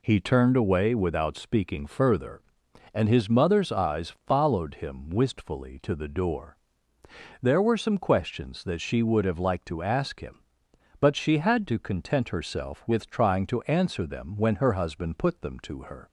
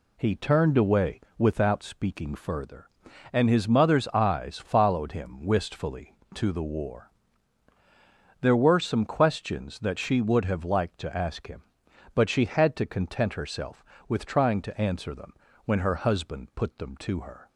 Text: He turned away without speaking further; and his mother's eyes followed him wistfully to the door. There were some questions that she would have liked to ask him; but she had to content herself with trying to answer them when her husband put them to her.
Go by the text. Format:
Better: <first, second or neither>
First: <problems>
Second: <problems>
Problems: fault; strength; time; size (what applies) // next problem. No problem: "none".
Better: first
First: none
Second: pauses between "away" and "without"; slight; at 1.2 s; 0.16 s long // says "war" for "door"; at 6.6 s // pauses between "them" and "when"; slight; at 15.3 s; 0.32 s long